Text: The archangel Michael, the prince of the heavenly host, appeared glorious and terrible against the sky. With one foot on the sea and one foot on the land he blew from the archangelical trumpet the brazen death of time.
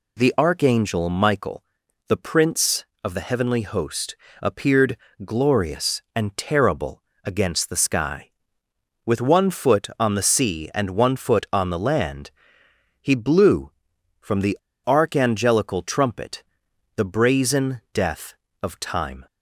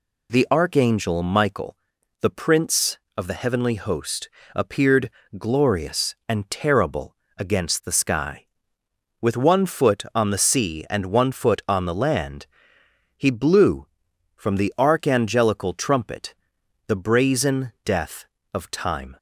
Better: second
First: pauses between "appeared" and "glorious"; slight; at 4.9 s; 0.26 s long // pauses between "terrible" and "against"; slight; at 7.0 s; 0.20 s long // pauses between "land" and "he"; noticeable; at 12.3 s; 0.68 s long // pauses between "the" and "archangelical"; slight; at 14.5 s; 0.26 s long // pauses between "trumpet" and "the"; noticeable; at 16.4 s; 0.54 s long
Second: pauses between "appeared" and "glorious"; slight; at 5.1 s; 0.26 s long // pauses between "terrible" and "against"; slight; at 7.1 s; 0.20 s long // pauses between "land" and "he"; noticeable; at 12.4 s; 0.68 s long // pauses between "trumpet" and "the"; noticeable; at 16.3 s; 0.54 s long

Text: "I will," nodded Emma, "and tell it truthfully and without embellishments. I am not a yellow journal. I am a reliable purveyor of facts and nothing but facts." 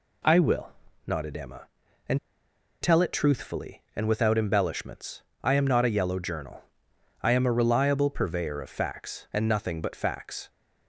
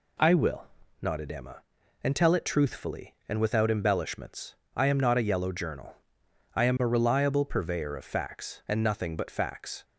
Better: second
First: pauses between "and" and "tell"; noticeable; at 2.1 s; 0.64 s long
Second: none

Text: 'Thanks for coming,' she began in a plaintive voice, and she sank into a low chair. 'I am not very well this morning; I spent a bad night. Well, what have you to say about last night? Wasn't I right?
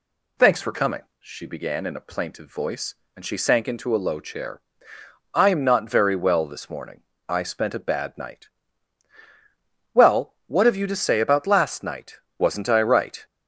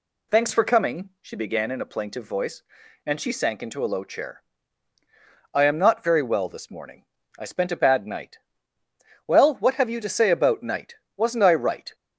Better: first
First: none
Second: skips "last"; at 10.6 s

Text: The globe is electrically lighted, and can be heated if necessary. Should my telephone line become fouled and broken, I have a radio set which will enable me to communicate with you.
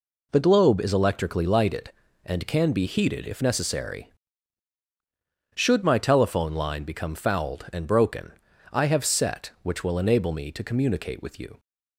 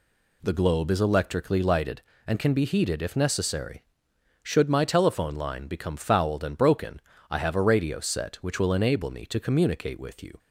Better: second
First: skips "a radio"; at 9.0 s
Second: none

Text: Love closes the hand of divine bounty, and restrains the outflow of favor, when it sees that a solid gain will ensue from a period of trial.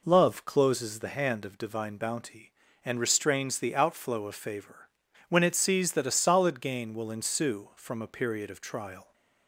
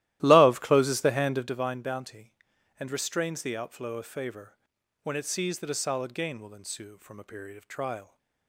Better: first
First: none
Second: starts louder than the rest; strong; until 1.7 s; 15 dB

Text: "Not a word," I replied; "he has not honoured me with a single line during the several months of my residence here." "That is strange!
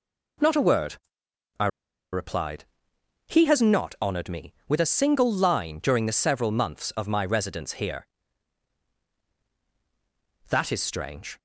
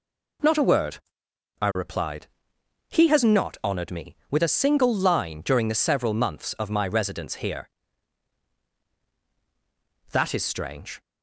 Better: second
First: pauses between "I" and "replied"; at 1.6 s; 0.45 s long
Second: none

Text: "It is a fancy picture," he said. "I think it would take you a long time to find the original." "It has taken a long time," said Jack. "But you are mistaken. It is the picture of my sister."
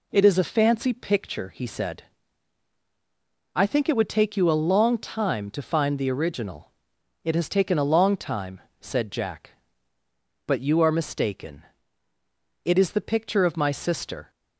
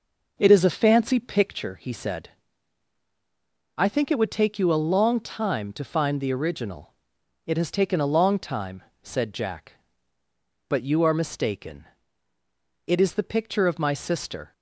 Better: first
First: none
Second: starts louder than the rest; noticeable; until 1.7 s; 5 dB

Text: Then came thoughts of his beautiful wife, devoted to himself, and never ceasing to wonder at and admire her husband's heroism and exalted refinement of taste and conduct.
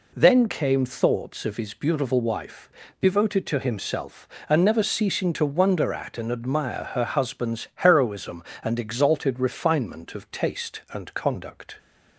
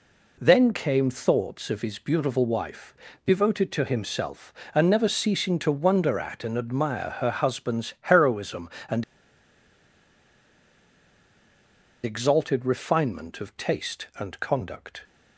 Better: first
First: none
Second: pauses between "and" and "exalted"; strong; at 9.0 s; 3.0 s long

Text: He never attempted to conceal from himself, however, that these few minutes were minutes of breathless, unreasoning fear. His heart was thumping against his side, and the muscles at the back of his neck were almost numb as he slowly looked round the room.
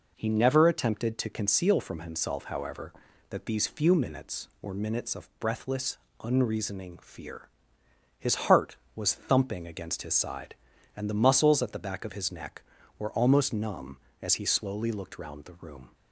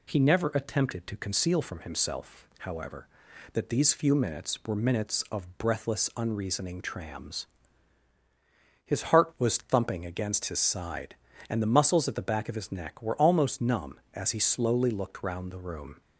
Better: first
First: none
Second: says "trams" for "fear"; at 6.8 s

